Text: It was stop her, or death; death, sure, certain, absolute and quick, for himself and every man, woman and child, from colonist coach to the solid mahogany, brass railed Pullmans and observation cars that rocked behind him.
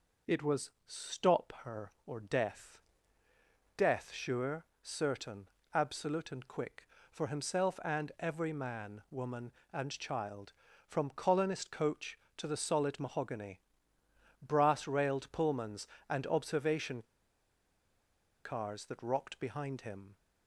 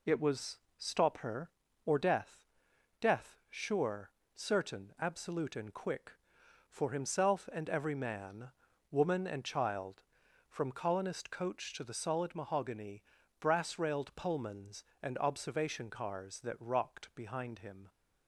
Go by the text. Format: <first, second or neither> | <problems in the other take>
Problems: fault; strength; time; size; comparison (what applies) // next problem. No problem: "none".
second | pauses between "was" and "stop"; slight; at 0.7 s; 0.16 s long; slight in the second // pauses between "observation" and "cars"; strong; at 17.0 s; 1.4 s long